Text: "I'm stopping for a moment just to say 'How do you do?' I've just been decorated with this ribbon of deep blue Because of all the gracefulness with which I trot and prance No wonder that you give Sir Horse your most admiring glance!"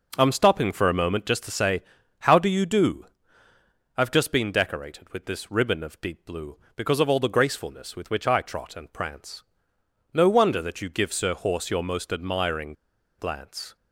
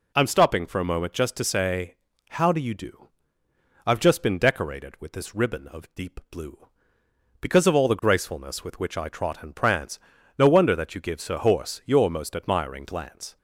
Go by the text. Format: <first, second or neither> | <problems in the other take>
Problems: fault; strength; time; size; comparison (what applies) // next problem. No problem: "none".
second | pauses between "say" and "How"; at 1.8 s; 0.38 s long; slight in the second // pauses between "prance" and "No"; noticeable; at 9.4 s; 0.72 s long; also in the second // pauses between "admiring" and "glance"; noticeable; at 12.7 s; 0.46 s long